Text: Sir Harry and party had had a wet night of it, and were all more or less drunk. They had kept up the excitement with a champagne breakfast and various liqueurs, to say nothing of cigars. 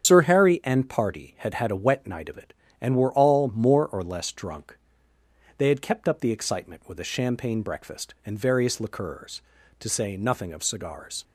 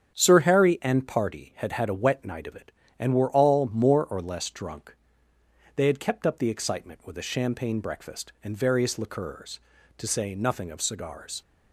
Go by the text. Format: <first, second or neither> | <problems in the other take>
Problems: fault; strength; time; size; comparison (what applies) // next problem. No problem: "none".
second | loses the start of "Sir"; at 0.0 s; 75 ms // starts louder than the rest; strong; until 1.1 s; 8.5 dB; strong in the second